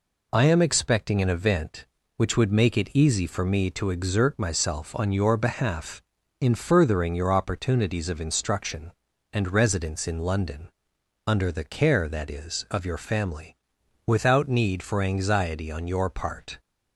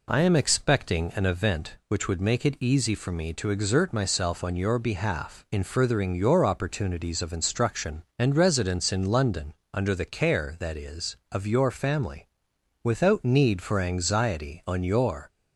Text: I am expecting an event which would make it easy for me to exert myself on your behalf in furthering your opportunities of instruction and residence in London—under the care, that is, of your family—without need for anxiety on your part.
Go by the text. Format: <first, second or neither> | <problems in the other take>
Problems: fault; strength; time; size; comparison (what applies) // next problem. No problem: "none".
first | stops before "part"; at 15.2 s